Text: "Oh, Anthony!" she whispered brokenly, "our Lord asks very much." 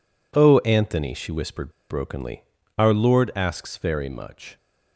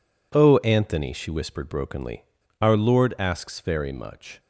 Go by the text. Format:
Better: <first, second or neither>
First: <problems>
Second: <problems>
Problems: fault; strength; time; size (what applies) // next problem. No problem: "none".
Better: second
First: pauses between "whispered" and "brokenly"; slight; at 1.7 s; 0.19 s long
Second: none